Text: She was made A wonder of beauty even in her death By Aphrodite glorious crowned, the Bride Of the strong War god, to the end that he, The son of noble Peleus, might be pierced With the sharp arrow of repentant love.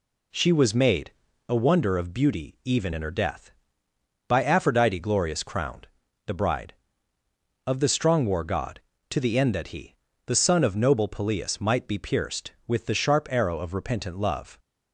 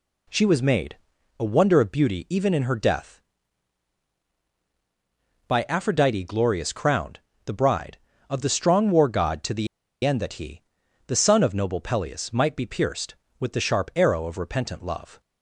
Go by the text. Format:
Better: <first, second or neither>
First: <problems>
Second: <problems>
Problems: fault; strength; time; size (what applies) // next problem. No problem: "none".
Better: first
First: pauses between "made" and "A"; at 1.1 s; 0.38 s long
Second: pauses between "made" and "A"; at 0.9 s; 0.42 s long // pauses between "the" and "end"; at 9.6 s; 0.37 s long